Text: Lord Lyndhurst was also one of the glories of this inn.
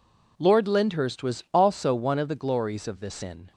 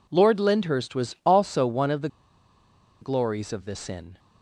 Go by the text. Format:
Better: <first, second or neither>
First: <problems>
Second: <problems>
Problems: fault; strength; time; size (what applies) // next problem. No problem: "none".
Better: first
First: none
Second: pauses between "the" and "glories"; noticeable; at 2.0 s; 0.94 s long